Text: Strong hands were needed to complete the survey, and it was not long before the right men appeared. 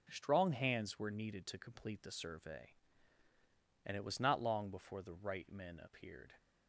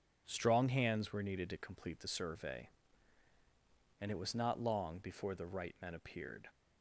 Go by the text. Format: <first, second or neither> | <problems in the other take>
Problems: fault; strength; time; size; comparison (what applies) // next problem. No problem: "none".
neither | none